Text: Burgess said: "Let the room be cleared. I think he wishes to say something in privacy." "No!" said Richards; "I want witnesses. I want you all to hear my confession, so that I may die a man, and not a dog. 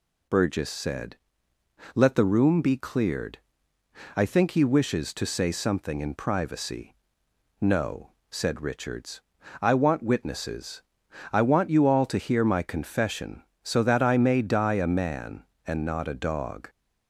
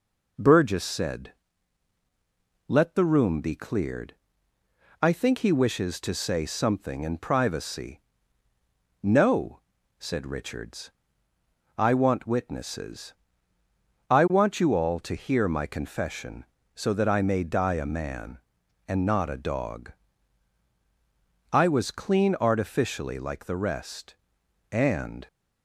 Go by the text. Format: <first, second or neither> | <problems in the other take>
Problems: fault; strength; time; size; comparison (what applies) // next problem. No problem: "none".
first | goes on to say "I was clean artificially like the rest and"; strong; from 21.5 s on; 3.7 s long